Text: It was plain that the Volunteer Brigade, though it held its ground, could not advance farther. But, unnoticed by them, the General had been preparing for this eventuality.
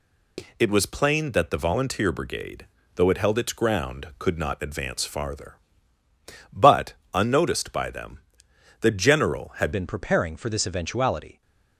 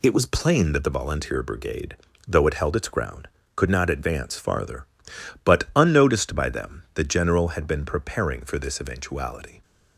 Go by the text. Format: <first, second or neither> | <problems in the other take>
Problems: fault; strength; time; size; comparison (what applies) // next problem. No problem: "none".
second | changes voice at "been"; from 9.7 s on; 1.7 s long